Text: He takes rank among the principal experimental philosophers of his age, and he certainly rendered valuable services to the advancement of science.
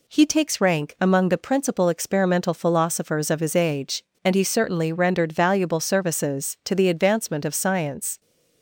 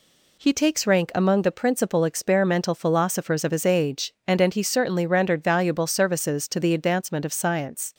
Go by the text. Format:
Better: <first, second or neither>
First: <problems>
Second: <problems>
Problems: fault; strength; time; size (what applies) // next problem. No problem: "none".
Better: first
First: none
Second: says "and" twice; at 4.3 s